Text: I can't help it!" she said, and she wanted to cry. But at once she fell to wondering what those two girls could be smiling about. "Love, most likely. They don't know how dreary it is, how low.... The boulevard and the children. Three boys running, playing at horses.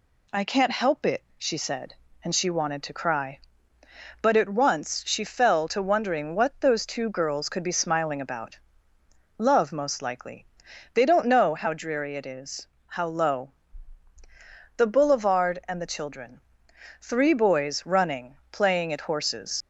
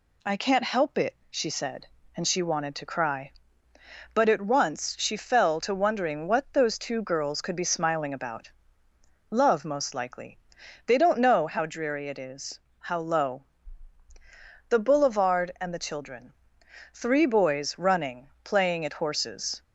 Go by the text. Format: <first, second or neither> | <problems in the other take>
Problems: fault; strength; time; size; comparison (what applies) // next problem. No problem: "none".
second | leaves "horses" unfinished; at 19.6 s; 95 ms